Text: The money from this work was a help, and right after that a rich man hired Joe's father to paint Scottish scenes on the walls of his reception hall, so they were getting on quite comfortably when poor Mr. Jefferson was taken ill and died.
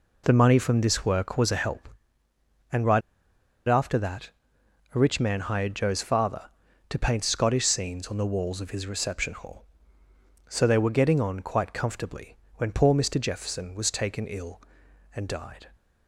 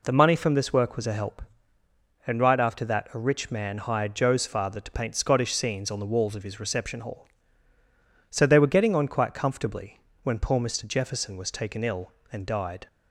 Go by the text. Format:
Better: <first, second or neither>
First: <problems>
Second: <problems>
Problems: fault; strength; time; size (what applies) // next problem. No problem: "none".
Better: second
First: pauses between "right" and "after"; noticeable; at 3.0 s; 0.66 s long // pauses between "that" and "a"; noticeable; at 4.2 s; 0.62 s long // pauses between "comfortably" and "when"; slight; at 12.3 s; 0.20 s long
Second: pauses between "comfortably" and "when"; slight; at 9.9 s; 0.24 s long